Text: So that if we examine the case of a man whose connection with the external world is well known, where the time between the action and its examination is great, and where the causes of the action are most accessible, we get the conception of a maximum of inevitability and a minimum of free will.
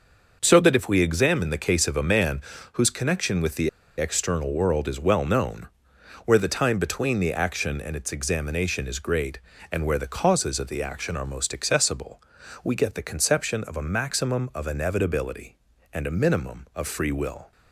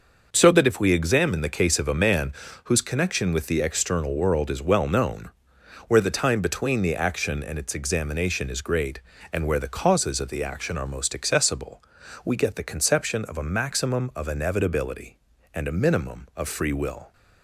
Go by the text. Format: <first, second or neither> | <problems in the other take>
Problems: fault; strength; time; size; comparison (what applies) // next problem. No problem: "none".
second | starts louder than the rest; noticeable; until 1.4 s; 6 dB // pauses between "man" and "whose"; slight; at 2.4 s; 0.32 s long; slight in the second // pauses between "the" and "external"; slight; at 3.6 s; 0.29 s long